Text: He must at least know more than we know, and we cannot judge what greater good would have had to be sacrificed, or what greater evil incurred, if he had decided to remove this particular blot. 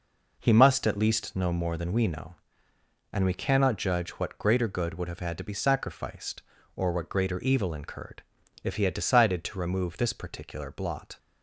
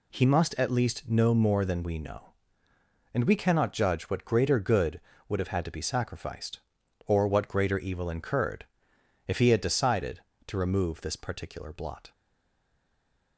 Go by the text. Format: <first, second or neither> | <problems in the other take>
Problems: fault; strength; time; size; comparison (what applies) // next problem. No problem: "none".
first | stays silent after the last word; noticeable; from 12.1 s on; 1.2 s long